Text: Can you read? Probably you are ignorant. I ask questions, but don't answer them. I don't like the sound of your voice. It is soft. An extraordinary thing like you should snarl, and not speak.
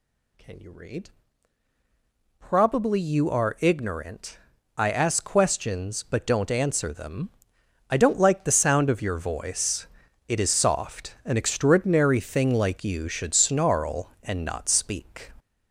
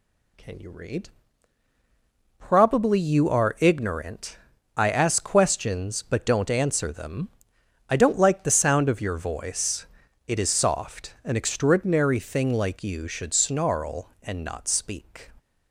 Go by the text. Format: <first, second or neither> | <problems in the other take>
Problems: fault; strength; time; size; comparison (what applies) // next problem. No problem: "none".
second | gets louder; noticeable; throughout; 4.5 dB